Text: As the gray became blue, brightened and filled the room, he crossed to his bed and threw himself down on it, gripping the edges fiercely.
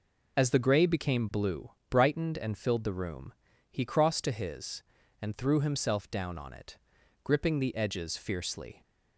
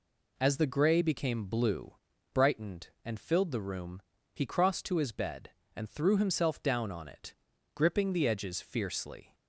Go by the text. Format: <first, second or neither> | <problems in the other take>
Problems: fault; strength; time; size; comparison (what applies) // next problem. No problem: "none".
second | skips "bed"; at 5.0 s